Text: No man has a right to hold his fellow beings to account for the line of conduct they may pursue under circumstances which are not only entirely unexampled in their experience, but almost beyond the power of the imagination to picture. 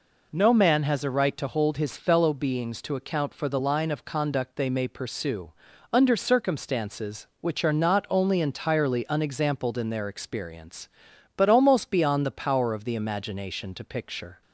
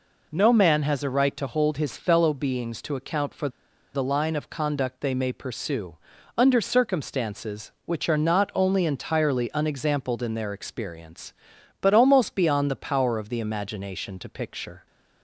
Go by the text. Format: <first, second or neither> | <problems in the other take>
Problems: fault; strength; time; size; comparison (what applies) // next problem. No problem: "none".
first | pauses between "for" and "the"; at 3.4 s; 0.45 s long // pauses between "pursue" and "under"; at 5.9 s; 0.40 s long; also in the first